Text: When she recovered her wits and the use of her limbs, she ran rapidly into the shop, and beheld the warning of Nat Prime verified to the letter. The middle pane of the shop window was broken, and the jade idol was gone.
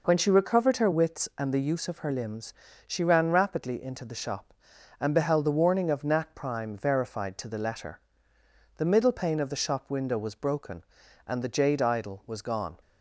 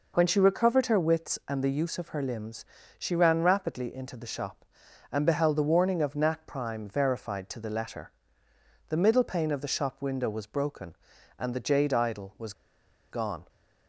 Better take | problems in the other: first | pauses between "was" and "gone"; noticeable; at 12.5 s; 0.58 s long

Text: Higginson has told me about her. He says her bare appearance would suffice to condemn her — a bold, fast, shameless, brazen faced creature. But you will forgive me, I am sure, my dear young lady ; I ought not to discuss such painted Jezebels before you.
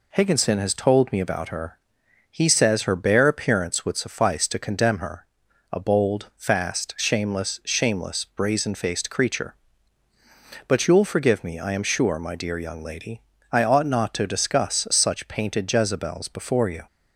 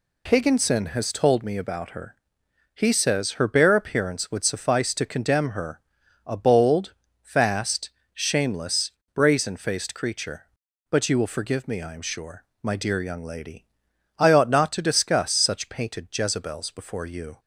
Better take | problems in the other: second | says "shameless" twice; at 7.6 s

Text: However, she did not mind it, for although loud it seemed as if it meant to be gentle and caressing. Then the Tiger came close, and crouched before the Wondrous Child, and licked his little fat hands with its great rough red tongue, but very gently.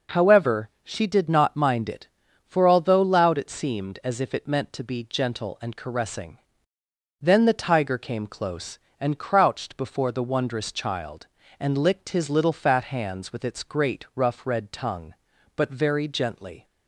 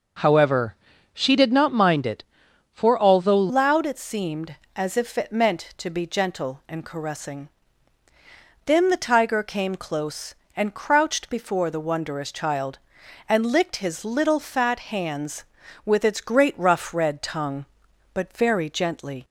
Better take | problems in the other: first | changes voice at "loud"; from 3.4 s on; 15.8 s long

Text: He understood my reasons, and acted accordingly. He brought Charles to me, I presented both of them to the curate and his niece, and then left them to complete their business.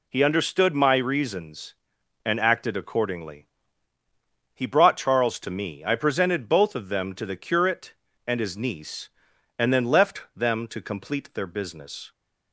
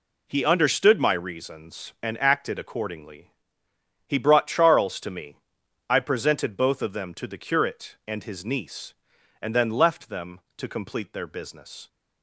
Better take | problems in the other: neither | none

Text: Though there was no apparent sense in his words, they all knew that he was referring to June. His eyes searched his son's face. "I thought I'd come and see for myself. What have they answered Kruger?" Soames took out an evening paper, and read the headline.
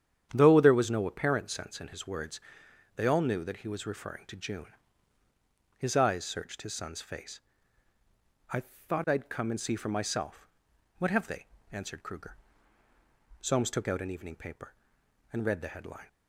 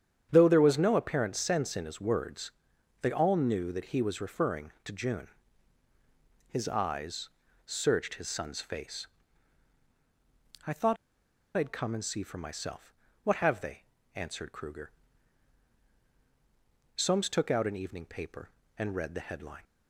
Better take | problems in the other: first | starts louder than the rest; strong; until 1.3 s; 9 dB; strong in the first // pauses between "eyes" and "searched"; slight; at 7.2 s; 0.36 s long // pauses between "thought" and "I'd"; noticeable; at 10.9 s; 0.60 s long // pauses between "they" and "answered"; slight; at 13.8 s; 0.32 s long; slight in the first

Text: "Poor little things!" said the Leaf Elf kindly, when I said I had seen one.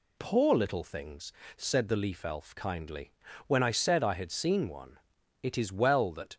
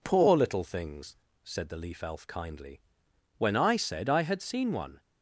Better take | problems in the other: second | goes on to say "It is well that"; noticeable; from 5.4 s on; 0.94 s long

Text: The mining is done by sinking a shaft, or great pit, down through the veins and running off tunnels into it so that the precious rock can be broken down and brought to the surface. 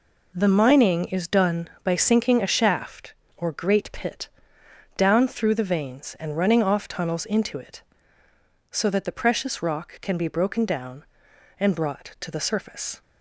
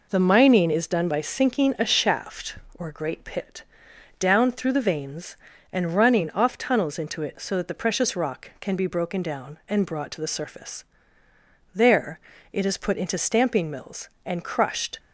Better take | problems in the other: first | goes on to say "There it is put into stamping mills and crushed"; strong; from 11.7 s on; 3.2 s long

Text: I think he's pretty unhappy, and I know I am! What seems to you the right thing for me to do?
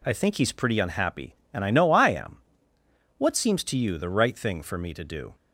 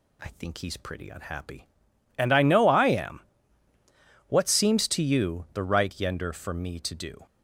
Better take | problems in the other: first | says "yender" for "thing"; at 5.9 s

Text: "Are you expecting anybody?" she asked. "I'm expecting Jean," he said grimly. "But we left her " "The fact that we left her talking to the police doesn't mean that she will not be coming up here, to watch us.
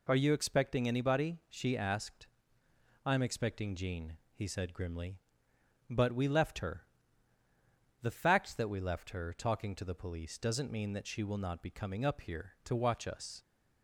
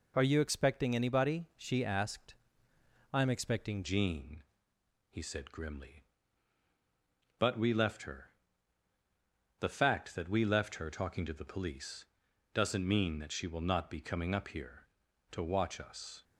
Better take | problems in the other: first | changes voice at "Jean"; from 3.8 s on; 12.4 s long // pauses between "police" and "doesn't"; noticeable; at 12.0 s; 0.50 s long

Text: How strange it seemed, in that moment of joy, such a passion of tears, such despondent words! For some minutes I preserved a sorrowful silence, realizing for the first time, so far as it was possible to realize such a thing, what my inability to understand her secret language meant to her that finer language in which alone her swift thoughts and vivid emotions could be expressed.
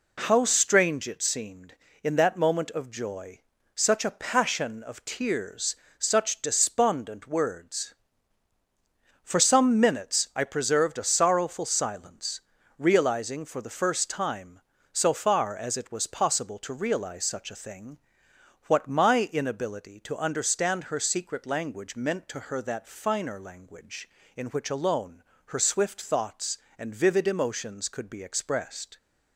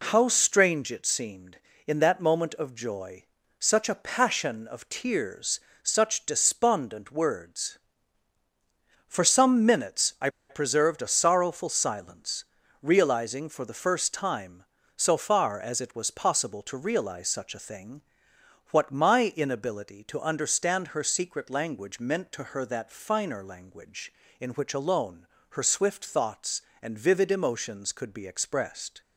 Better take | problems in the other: first | pauses between "I" and "preserved"; slight; at 10.2 s; 0.21 s long // pauses between "alone" and "her"; slight; at 25.2 s; 0.22 s long; slight in the first

